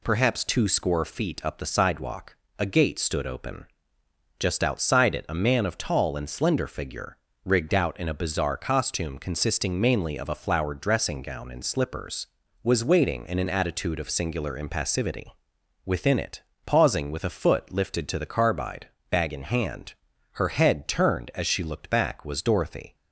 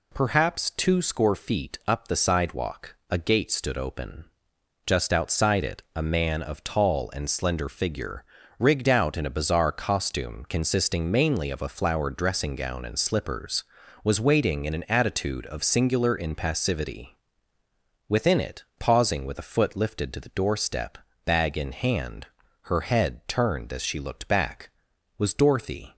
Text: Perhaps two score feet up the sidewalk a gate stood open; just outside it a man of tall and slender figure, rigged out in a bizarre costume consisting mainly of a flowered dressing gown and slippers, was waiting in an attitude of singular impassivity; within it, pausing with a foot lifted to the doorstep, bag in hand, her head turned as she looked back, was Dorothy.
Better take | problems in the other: second | pauses between "sidewalk" and "a"; slight; at 2.3 s; 0.24 s long // says "carbide" for "doorstep"; at 18.2 s

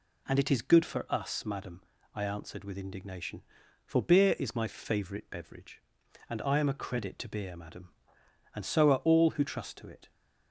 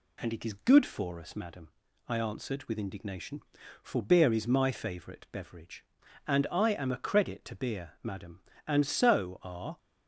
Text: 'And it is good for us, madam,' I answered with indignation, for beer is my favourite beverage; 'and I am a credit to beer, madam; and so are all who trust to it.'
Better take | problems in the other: first | stops before "all who trust to it"; at 9.7 s

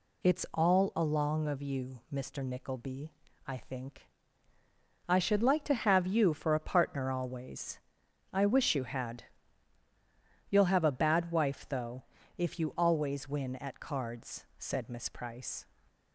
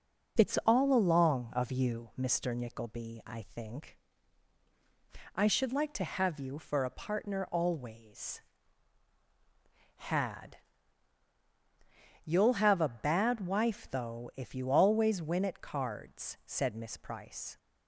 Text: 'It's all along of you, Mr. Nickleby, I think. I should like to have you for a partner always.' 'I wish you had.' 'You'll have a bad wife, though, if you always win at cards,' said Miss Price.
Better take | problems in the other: first | skips "I wish you"; at 9.1 s

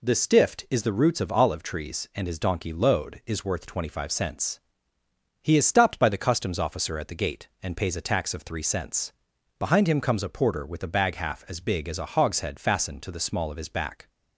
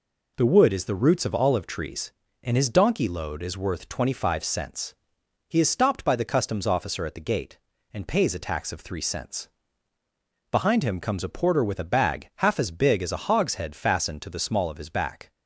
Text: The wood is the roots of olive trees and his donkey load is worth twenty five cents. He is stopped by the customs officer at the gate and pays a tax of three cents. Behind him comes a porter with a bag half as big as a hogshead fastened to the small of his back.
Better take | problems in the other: second | says "stift" for "wood"; at 0.1 s

